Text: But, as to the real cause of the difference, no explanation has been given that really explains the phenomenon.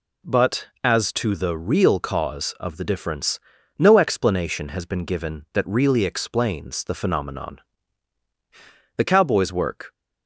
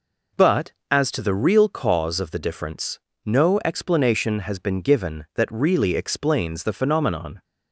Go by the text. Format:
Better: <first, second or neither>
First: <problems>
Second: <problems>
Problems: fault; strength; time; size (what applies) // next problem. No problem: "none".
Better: second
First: goes on to say "The cowboy's work"; noticeable; from 8.9 s on; 0.96 s long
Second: none